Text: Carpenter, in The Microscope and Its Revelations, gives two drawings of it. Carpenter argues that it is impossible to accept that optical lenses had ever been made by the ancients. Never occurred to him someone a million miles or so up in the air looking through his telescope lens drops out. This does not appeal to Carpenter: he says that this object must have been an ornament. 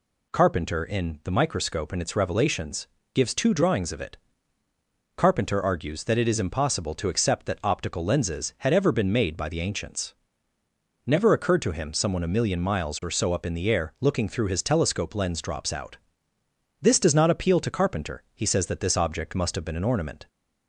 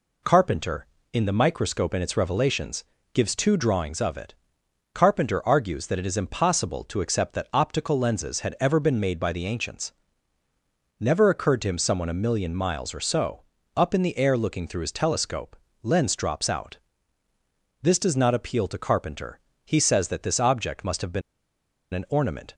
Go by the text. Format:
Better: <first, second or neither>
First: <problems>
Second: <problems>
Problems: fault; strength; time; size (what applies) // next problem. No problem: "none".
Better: first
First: none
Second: pauses between "so" and "up"; slight; at 13.4 s; 0.34 s long // pauses between "telescope" and "lens"; slight; at 15.5 s; 0.24 s long // pauses between "been" and "an"; noticeable; at 21.2 s; 0.72 s long